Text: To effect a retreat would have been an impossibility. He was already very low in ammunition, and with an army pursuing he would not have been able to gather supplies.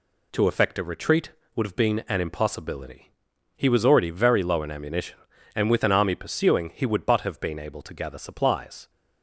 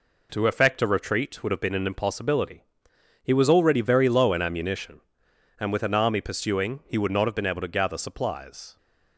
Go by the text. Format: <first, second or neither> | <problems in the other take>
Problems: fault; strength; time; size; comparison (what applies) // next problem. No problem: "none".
second | says "but" for "not"; at 7.0 s